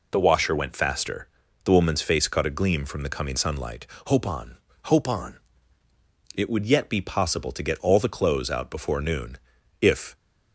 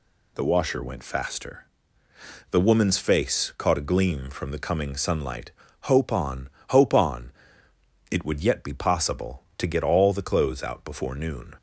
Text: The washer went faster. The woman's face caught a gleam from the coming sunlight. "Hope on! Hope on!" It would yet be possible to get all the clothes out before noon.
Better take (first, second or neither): second